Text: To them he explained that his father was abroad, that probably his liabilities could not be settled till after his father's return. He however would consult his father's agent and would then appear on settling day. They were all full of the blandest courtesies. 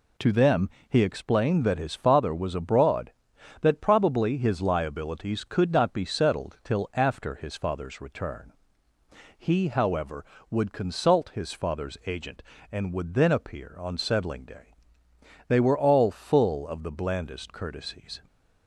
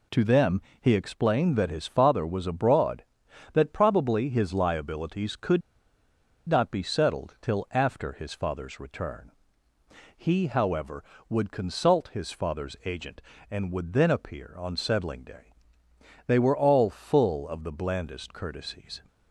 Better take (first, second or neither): first